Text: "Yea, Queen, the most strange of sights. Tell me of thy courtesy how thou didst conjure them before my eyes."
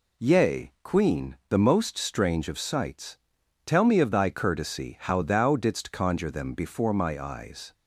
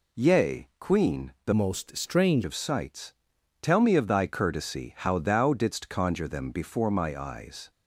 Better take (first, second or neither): first